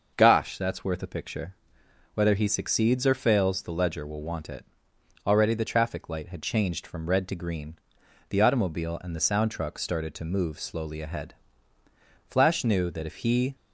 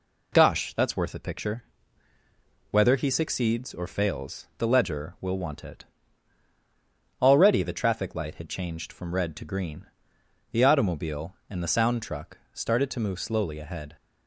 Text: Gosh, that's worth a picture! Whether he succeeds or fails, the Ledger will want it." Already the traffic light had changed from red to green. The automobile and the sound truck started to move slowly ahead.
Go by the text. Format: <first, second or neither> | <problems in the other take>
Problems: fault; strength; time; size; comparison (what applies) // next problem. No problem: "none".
second | starts louder than the rest; noticeable; until 1.1 s; 6 dB // goes on to say "Flash knew that if he"; noticeable; from 12.2 s on; 1.2 s long